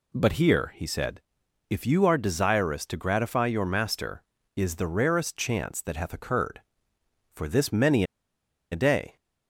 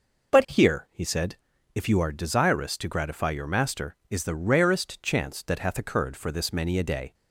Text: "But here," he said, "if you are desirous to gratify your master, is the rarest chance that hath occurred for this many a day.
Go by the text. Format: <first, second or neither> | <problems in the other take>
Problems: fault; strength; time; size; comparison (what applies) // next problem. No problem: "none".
second | pauses between "many" and "a"; noticeable; at 8.0 s; 0.67 s long